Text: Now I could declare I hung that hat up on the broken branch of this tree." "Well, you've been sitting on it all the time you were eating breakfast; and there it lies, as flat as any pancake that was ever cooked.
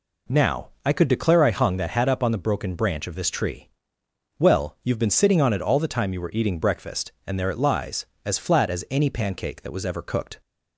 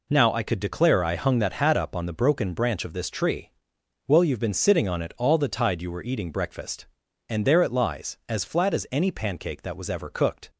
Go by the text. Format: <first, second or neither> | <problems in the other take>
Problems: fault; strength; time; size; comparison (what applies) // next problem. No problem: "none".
first | says "tide" for "time"; at 5.4 s